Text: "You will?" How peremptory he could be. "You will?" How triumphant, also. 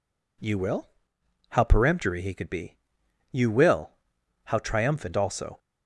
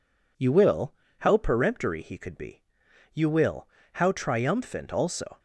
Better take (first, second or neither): neither